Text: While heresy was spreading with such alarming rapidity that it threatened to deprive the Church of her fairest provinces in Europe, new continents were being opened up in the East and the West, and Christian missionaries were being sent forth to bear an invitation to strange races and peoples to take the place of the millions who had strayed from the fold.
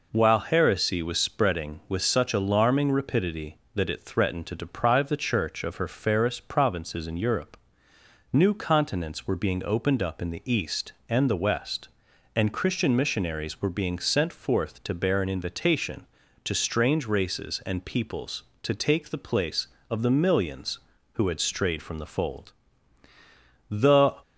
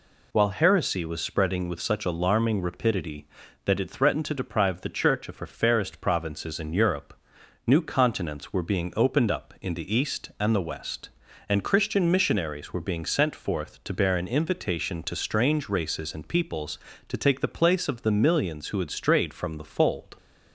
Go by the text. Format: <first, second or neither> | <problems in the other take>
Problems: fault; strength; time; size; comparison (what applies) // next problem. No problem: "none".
second | goes on to say "The"; from 23.6 s on; 0.50 s long